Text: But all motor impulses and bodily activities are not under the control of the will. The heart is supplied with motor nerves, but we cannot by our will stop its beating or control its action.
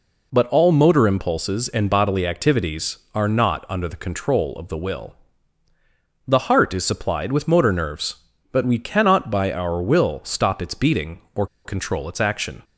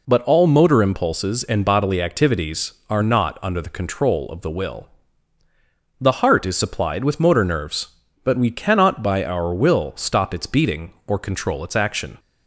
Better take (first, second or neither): second